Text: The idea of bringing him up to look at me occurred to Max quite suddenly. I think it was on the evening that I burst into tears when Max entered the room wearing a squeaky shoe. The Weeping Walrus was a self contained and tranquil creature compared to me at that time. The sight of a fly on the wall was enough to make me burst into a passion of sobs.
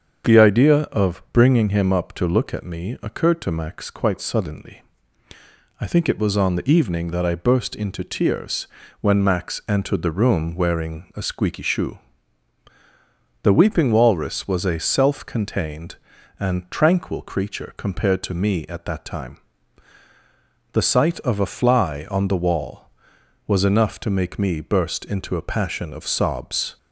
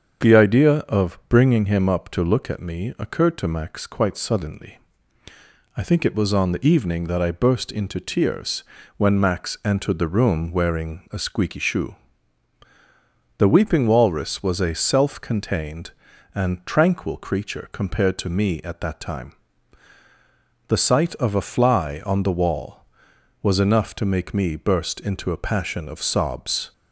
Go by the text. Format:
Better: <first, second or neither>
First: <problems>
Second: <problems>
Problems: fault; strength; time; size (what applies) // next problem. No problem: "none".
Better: neither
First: starts louder than the rest; strong; until 1.4 s; 7 dB // pauses between "tears" and "when"; slight; at 8.6 s; 0.36 s long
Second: starts louder than the rest; strong; until 1.3 s; 7 dB // pauses between "tears" and "when"; slight; at 8.6 s; 0.36 s long